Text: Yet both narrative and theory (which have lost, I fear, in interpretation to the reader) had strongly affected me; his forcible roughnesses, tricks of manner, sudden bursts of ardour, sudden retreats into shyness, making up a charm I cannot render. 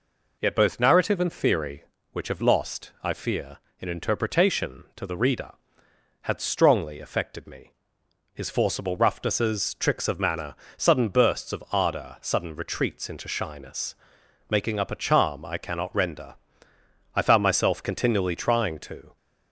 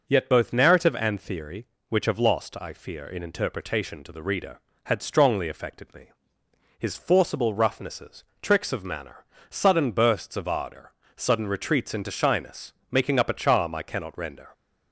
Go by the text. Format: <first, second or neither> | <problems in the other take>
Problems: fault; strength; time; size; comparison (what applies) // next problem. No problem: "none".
second | goes on to say "I found myself continually trying to"; strong; from 17.1 s on; 2.0 s long